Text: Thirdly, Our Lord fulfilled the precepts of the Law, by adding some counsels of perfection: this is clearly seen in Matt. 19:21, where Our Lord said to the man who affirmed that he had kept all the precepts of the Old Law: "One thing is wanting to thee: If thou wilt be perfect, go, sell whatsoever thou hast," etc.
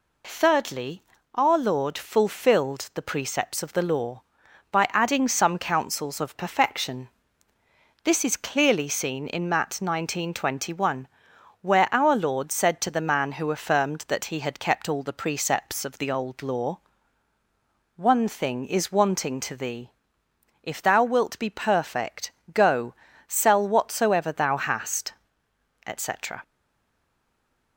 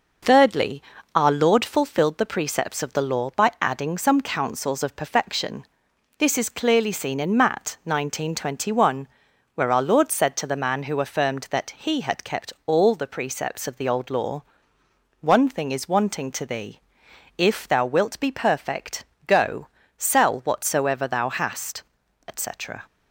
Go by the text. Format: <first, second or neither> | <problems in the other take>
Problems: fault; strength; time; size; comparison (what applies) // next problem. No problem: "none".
second | stays silent after the last word; noticeable; from 26.4 s on; 1.3 s long